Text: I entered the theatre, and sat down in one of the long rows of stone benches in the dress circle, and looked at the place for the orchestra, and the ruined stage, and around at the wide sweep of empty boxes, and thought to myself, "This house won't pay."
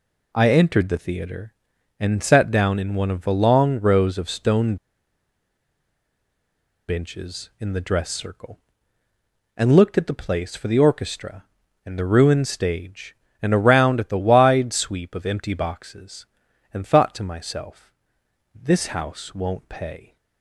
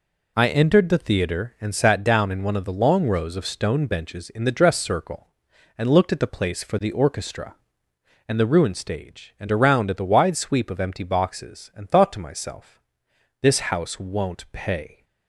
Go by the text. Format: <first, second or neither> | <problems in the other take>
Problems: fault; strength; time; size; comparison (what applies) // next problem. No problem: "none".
second | pauses between "stone" and "benches"; strong; at 4.7 s; 2.1 s long